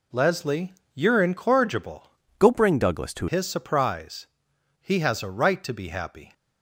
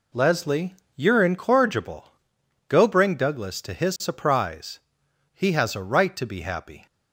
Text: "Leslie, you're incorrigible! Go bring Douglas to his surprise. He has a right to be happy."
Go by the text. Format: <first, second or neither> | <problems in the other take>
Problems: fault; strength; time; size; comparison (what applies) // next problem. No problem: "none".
second | changes voice from "Go" to "to"; from 2.3 to 3.2 s; 0.9 s long